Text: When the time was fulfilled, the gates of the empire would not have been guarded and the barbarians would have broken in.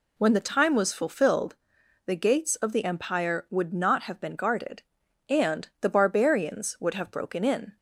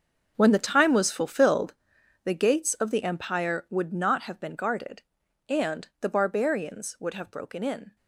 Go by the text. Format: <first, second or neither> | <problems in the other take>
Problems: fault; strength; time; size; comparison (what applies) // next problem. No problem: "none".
first | gets quieter; strong; throughout; 14 dB